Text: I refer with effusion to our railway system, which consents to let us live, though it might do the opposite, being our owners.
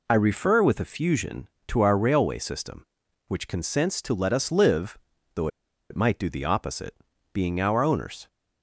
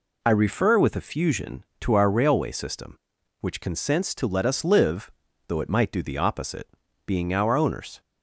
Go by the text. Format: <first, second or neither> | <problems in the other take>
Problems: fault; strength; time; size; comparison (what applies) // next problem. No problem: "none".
second | pauses between "though" and "it"; at 5.4 s; 0.42 s long